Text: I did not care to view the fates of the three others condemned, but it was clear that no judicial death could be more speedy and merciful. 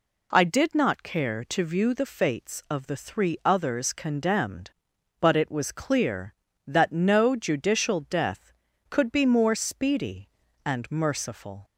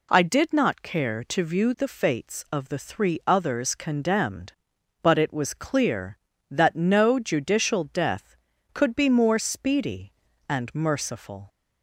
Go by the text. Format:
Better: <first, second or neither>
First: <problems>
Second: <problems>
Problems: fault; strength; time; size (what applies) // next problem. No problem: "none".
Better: neither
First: none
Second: none